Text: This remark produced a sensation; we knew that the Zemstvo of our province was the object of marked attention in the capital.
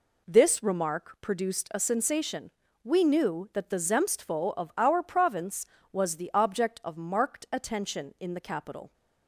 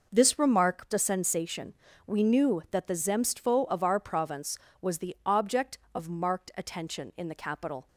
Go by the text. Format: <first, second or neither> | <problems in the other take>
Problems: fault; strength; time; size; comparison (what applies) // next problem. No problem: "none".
first | skips "produced"; at 0.9 s